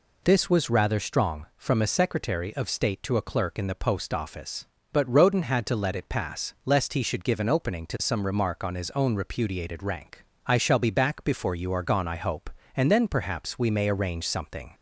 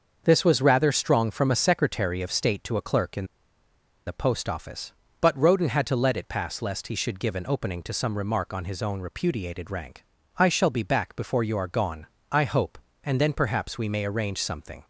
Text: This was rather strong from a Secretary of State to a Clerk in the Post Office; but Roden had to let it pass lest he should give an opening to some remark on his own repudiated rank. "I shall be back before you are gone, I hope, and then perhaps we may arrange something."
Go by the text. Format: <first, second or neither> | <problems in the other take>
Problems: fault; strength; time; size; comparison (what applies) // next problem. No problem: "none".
first | starts louder than the rest; until 1.2 s; 6.5 dB // pauses between "in" and "the"; noticeable; at 3.2 s; 0.80 s long